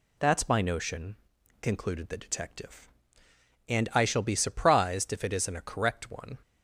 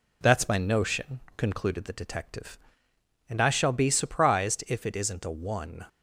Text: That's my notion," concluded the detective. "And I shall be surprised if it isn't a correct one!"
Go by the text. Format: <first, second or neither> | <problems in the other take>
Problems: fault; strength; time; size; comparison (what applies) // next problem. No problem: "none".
first | skips "correct"; at 5.3 s